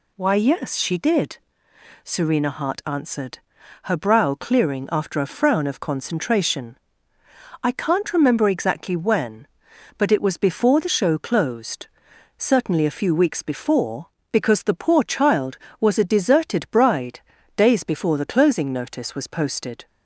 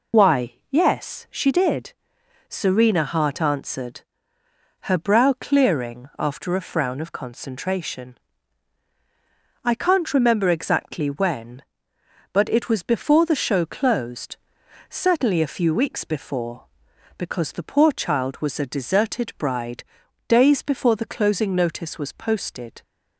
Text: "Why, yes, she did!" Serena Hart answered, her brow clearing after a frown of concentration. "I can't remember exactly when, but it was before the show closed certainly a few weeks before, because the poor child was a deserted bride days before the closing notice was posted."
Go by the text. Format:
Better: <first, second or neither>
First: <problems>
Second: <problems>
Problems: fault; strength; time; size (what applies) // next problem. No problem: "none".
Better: first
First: pauses between "closed" and "certainly"; noticeable; at 11.8 s; 0.50 s long // pauses between "bride" and "days"; at 17.1 s; 0.38 s long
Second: loses the start of "Why"; at 0.1 s; 60 ms // pauses between "closed" and "certainly"; noticeable; at 14.3 s; 0.52 s long // pauses between "bride" and "days"; at 19.8 s; 0.42 s long